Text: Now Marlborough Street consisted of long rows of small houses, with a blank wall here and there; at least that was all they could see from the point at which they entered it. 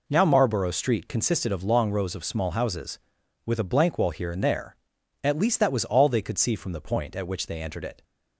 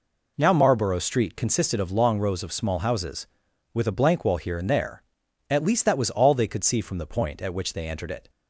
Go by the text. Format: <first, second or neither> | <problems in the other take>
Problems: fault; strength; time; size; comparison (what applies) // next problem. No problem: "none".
neither | none